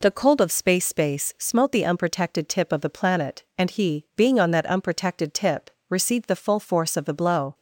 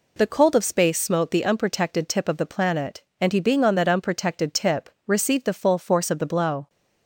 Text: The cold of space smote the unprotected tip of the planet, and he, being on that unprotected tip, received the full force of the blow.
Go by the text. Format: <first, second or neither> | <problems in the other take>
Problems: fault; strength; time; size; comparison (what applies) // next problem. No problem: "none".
second | says "space" twice; at 0.8 s